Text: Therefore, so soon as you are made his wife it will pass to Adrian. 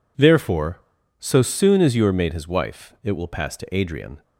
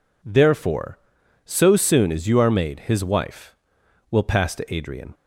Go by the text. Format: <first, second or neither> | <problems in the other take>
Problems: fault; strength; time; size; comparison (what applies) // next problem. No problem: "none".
first | skips "it"; at 3.8 s